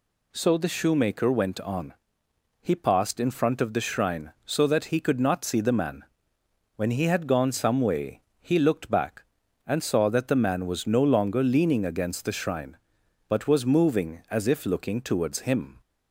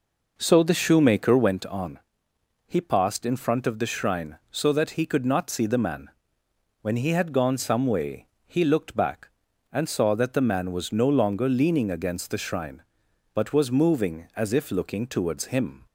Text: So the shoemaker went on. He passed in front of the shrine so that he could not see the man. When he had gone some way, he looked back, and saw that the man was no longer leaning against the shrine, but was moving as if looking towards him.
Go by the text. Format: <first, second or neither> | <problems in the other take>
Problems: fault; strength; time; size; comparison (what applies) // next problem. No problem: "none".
first | starts louder than the rest; noticeable; until 1.7 s; 5 dB